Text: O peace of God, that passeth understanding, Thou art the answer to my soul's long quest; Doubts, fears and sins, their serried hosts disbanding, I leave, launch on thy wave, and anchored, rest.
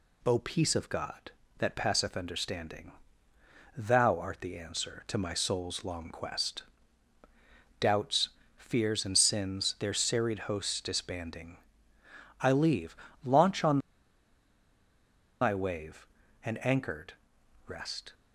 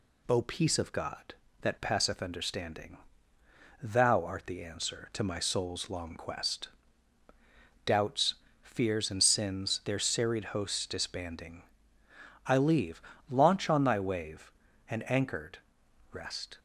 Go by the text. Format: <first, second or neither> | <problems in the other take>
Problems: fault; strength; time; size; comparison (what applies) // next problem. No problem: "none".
second | pauses between "on" and "thy"; strong; at 13.7 s; 1.6 s long